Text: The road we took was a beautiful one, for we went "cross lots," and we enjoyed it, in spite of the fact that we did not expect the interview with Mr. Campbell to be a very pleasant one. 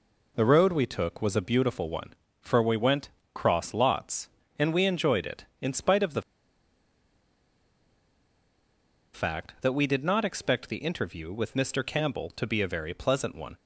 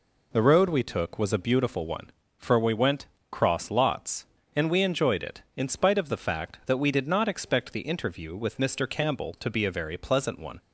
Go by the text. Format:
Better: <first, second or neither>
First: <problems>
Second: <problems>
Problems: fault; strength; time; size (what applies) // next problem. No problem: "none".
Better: second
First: pauses between "went" and "cross"; slight; at 3.0 s; 0.26 s long // pauses between "the" and "fact"; strong; at 6.2 s; 2.9 s long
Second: pauses between "went" and "cross"; slight; at 3.0 s; 0.26 s long